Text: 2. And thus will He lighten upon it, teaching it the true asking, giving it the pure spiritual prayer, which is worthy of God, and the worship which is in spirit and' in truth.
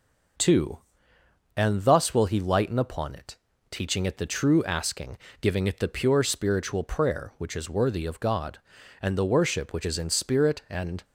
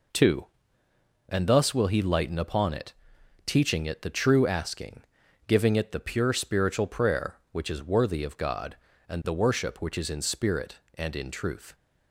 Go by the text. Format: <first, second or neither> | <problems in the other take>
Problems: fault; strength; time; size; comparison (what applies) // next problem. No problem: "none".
second | stops before "in truth"; at 11.0 s